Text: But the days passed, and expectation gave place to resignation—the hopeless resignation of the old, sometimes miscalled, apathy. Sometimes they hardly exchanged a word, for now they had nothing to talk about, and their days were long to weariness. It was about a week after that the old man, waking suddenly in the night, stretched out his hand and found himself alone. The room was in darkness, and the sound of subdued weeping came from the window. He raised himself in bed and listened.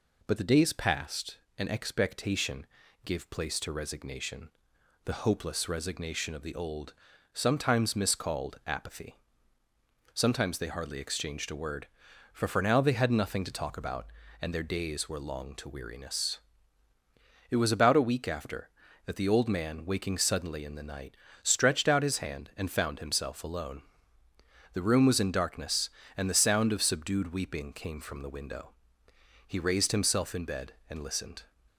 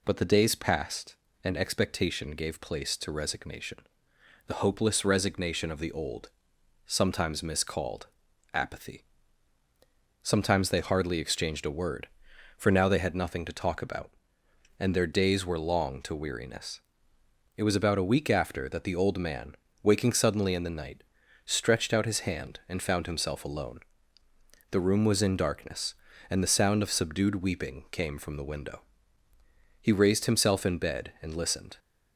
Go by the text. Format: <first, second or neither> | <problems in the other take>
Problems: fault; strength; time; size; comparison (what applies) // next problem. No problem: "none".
second | pauses between "expectation" and "gave"; at 2.6 s; 0.38 s long // says "for" twice; at 12.4 s